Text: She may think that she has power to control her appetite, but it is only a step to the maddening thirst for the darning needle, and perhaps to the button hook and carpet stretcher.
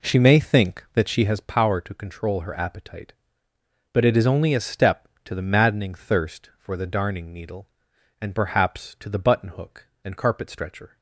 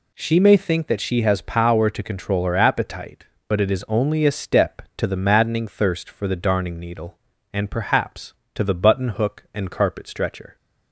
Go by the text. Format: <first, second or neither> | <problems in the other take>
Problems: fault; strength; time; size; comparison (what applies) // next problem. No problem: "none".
second | starts louder than the rest; slight; until 1.4 s; 3.5 dB